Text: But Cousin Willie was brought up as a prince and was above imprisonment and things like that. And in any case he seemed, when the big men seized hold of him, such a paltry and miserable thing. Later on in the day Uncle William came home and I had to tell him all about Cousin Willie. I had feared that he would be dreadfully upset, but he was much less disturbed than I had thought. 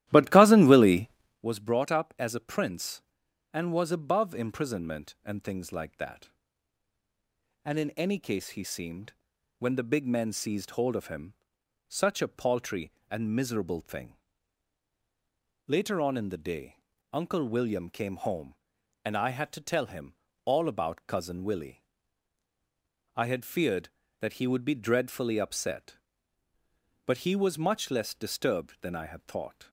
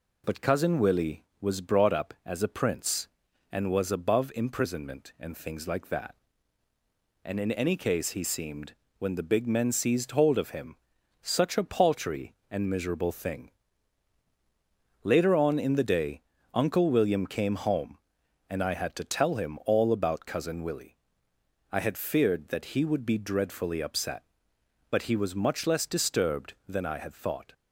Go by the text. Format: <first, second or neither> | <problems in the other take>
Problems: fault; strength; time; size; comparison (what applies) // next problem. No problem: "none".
second | starts louder than the rest; strong; until 1.4 s; 14 dB // pauses between "day" and "Uncle"; slight; at 16.7 s; 0.34 s long; slight in the second // pauses between "him" and "all"; slight; at 20.1 s; 0.32 s long